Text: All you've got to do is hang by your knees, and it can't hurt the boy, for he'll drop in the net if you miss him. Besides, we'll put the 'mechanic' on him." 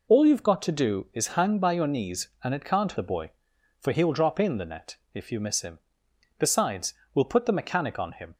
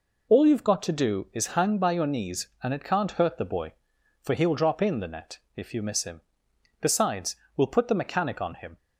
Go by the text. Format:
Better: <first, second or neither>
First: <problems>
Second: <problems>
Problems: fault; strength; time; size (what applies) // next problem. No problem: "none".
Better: second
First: skips "hurt"; at 2.9 s // pauses between "net" and "if"; slight; at 4.9 s; 0.18 s long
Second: pauses between "net" and "if"; slight; at 5.3 s; 0.18 s long